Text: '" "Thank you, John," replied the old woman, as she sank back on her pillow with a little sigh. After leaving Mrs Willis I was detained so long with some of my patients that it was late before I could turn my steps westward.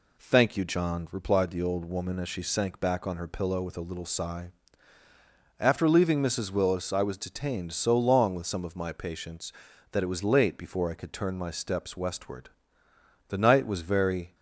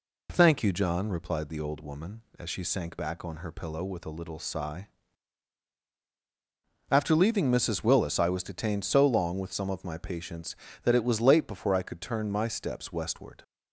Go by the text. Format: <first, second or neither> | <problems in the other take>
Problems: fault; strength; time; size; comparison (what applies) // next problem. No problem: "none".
second | goes on to say "The night was very"; noticeable; from 13.2 s on; 1.0 s long